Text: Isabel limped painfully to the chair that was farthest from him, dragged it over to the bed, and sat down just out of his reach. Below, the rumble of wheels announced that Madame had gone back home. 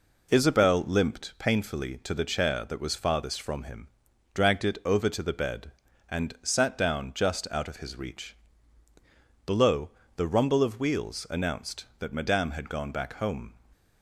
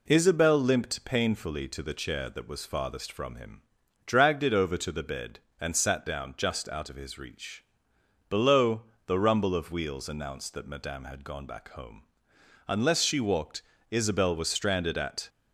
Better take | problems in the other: first | goes on to say "Unless she walked Isabel was stranded at"; strong; from 12.6 s on; 2.6 s long

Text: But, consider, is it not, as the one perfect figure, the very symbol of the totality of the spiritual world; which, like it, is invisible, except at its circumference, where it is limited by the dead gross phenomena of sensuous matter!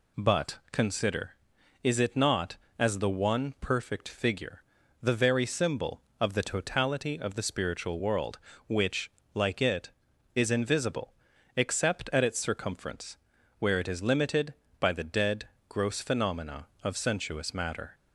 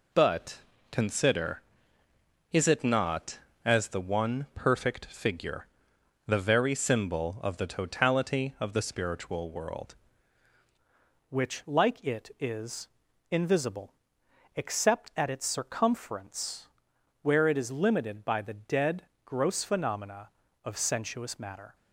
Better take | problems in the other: first | changes voice at "which"; from 11.2 s on; 10.5 s long // pauses between "is" and "invisible"; at 12.8 s; 0.42 s long // pauses between "dead" and "gross"; slight; at 19.0 s; 0.22 s long; slight in the first

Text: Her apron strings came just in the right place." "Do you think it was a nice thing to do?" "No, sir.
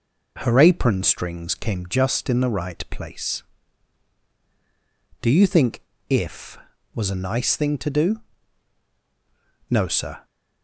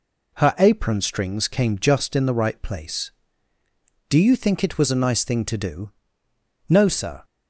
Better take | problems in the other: second | says "if" for "it"; at 6.0 s

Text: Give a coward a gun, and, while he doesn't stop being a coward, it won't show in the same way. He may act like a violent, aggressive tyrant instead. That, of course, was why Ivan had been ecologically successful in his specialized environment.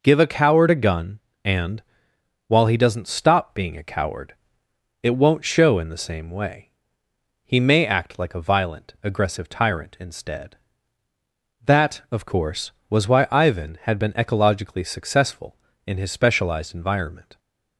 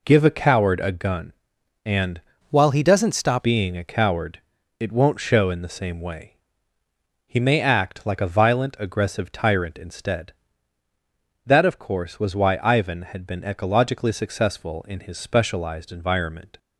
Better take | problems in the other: first | changes voice from "while" to "stop"; from 2.4 to 3.4 s; 1.0 s long

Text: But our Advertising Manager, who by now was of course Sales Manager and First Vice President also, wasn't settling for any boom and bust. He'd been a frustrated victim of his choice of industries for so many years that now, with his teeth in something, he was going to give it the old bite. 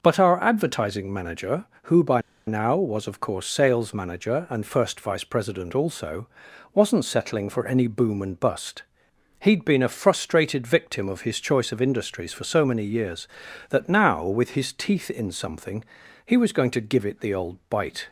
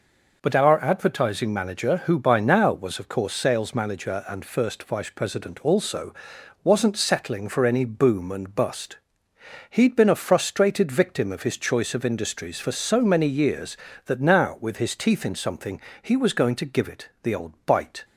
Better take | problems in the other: second | pauses between "by" and "now"; slight; at 2.2 s; 0.26 s long

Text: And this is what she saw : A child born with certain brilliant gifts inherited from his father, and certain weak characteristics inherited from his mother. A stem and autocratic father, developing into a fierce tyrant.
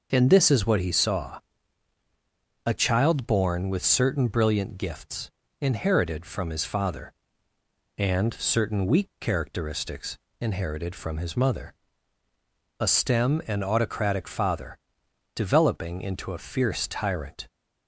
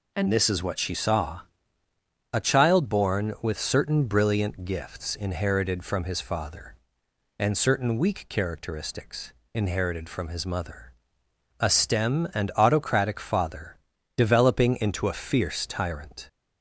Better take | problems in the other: second | says "he" for "she"; at 0.8 s // pauses between "gifts" and "inherited"; slight; at 5.3 s; 0.30 s long // pauses between "characteristics" and "inherited"; slight; at 10.1 s; 0.24 s long; slight in the second

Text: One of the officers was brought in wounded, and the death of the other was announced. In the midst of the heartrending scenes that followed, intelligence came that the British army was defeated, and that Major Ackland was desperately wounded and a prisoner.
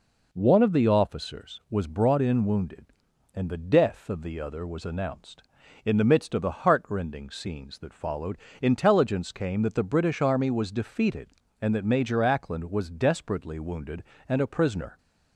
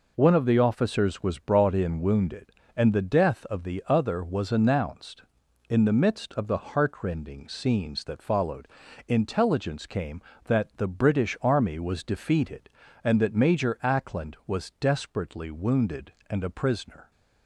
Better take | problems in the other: neither | none

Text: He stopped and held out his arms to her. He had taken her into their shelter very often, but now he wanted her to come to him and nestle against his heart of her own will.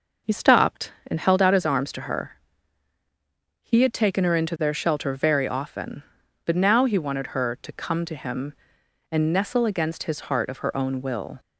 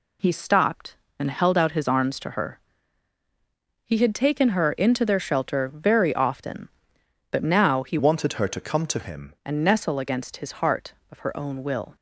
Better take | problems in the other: first | changes voice from "wanted" to "him"; from 7.9 to 9.3 s; 1.4 s long

